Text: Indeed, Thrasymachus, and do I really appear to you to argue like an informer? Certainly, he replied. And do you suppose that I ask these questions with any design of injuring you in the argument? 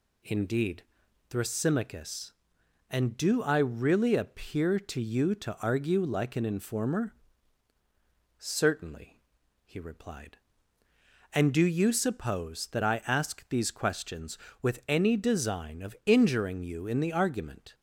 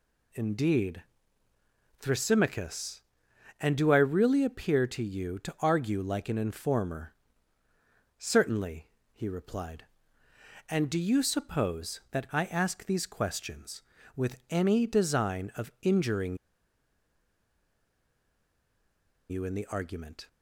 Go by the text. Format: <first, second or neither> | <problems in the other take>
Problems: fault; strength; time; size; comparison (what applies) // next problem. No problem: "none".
first | pauses between "injuring" and "you"; strong; at 16.3 s; 2.9 s long